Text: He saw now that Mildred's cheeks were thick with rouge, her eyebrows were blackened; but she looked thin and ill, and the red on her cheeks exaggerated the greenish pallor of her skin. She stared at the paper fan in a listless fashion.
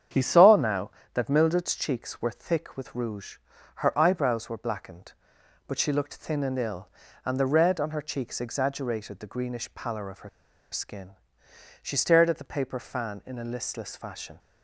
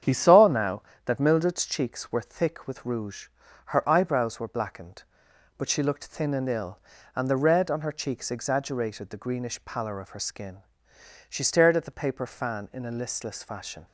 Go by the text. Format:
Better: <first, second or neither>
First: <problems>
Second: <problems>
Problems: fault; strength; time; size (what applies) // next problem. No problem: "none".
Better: second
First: starts louder than the rest; strong; until 1.3 s; 8.5 dB // pauses between "her" and "skin"; at 10.2 s; 0.42 s long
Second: starts louder than the rest; strong; until 1.3 s; 8.5 dB